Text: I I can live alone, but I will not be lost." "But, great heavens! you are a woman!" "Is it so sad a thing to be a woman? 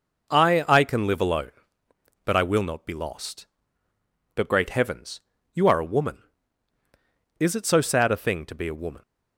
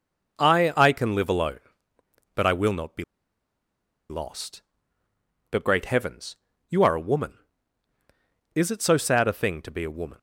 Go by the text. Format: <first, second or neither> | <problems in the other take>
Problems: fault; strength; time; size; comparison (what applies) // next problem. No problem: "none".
first | pauses between "be" and "lost"; at 3.0 s; 1.0 s long